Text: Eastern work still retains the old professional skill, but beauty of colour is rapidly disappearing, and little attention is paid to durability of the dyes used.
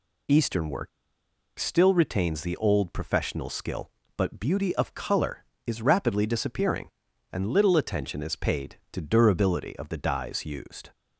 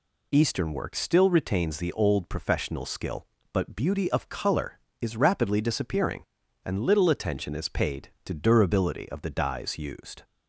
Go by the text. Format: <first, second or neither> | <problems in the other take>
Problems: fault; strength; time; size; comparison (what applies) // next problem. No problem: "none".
second | pauses between "work" and "still"; noticeable; at 0.8 s; 0.70 s long